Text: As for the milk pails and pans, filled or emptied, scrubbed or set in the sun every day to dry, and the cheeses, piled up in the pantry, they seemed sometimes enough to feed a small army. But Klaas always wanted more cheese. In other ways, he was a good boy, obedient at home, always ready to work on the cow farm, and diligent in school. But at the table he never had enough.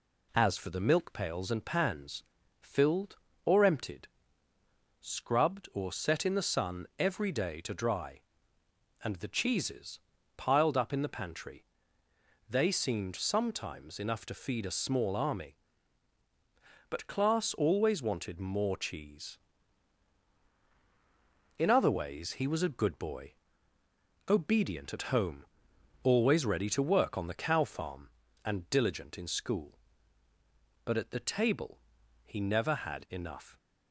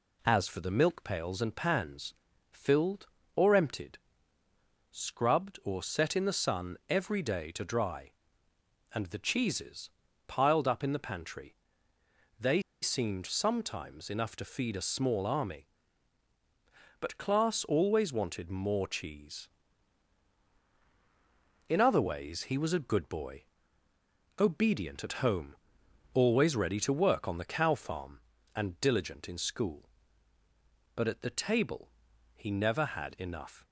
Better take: first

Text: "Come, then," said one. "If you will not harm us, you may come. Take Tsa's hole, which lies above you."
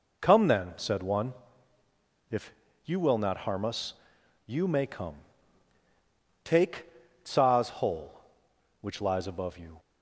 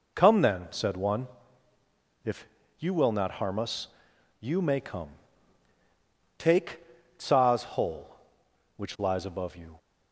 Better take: neither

